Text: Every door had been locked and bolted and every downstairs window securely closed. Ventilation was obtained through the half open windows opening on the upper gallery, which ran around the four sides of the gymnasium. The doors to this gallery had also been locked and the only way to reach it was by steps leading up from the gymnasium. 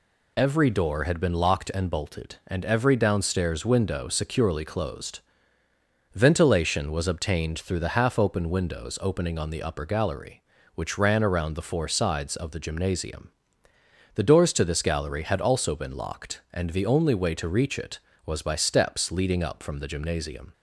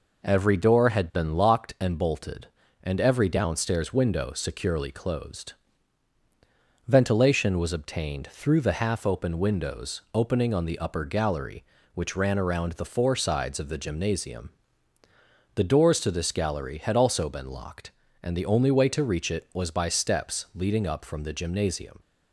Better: neither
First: none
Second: none

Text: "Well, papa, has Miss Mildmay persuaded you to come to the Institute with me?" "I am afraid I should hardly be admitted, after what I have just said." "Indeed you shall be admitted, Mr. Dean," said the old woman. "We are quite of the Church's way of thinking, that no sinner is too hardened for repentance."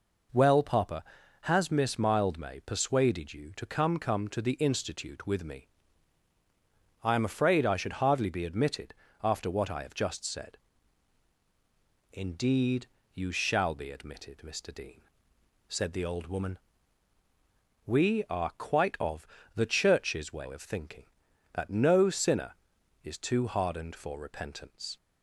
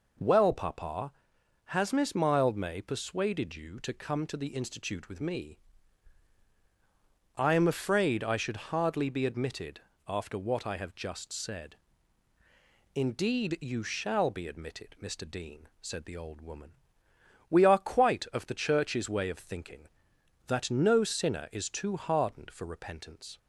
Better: second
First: says "come" twice; at 3.9 s // pauses between "Indeed" and "you"; slight; at 12.8 s; 0.26 s long // pauses between "of" and "the"; slight; at 19.2 s; 0.30 s long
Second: none

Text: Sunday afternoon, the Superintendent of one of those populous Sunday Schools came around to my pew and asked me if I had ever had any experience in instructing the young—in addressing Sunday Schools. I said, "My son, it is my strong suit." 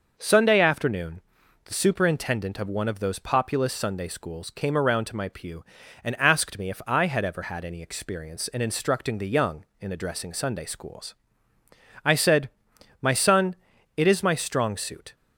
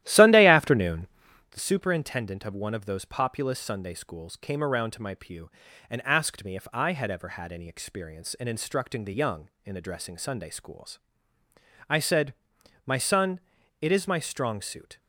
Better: first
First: none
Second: starts louder than the rest; strong; until 1.5 s; 13.5 dB

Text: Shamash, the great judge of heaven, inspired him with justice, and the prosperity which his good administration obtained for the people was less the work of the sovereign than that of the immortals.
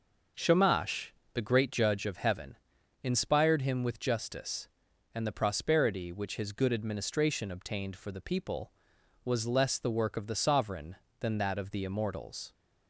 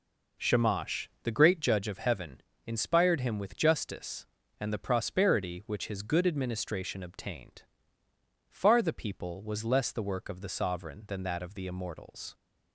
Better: first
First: none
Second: says "far" for "for"; at 8.4 s

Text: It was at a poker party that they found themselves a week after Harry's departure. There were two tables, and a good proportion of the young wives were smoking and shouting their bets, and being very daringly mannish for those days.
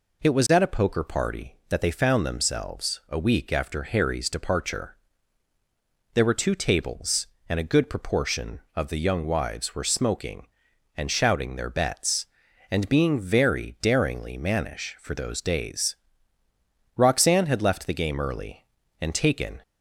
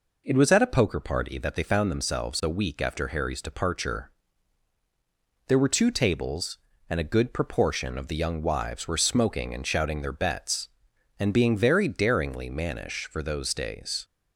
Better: second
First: goes on to say "Roxanne had left the game early and taken"; strong; from 16.9 s on; 2.6 s long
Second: none

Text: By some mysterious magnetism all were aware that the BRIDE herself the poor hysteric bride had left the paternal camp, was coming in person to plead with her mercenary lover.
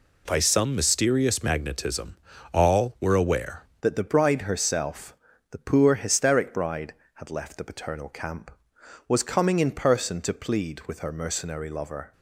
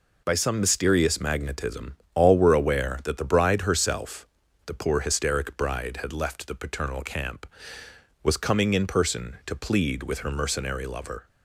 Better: second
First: pauses between "magnetism" and "all"; slight; at 2.1 s; 0.36 s long // changes voice at "that"; from 3.8 s on; 8.3 s long // pauses between "herself" and "the"; slight; at 5.1 s; 0.36 s long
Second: pauses between "magnetism" and "all"; slight; at 1.9 s; 0.18 s long // pauses between "herself" and "the"; at 4.2 s; 0.40 s long

